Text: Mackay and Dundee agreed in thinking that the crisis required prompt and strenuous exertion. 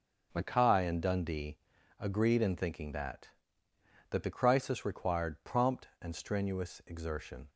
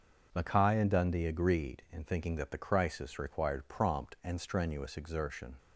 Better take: second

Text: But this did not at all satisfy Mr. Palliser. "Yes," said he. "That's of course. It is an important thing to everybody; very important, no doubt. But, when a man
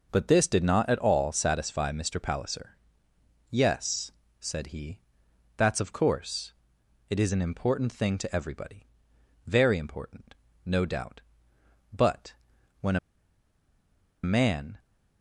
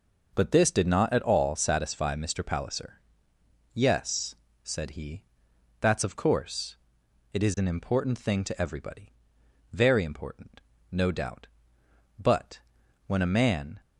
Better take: second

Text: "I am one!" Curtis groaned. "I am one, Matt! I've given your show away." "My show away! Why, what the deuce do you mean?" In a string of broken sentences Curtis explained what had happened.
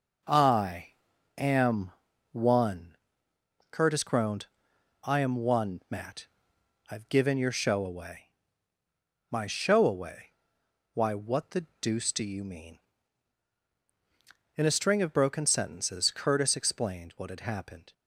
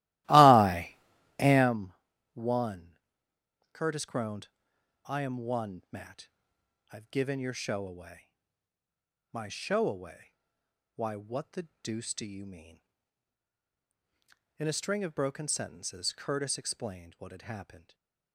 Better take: first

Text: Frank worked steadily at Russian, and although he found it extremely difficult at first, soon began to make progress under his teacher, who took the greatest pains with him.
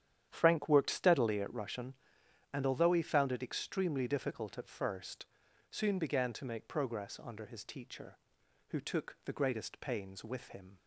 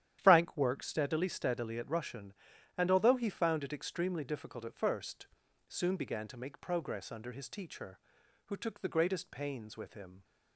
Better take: first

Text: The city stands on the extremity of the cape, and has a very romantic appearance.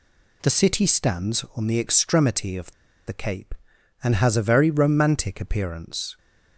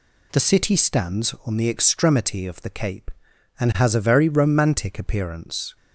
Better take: second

